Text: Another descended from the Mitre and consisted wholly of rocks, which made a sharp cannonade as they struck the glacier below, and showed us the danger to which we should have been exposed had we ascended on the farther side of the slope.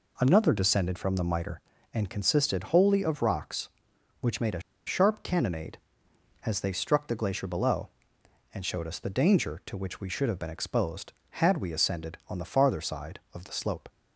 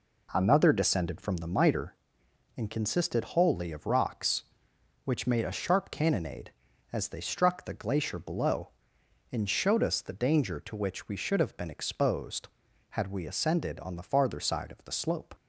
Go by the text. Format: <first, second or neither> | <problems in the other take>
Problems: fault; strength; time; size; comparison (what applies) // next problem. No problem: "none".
second | pauses between "a" and "sharp"; slight; at 4.6 s; 0.25 s long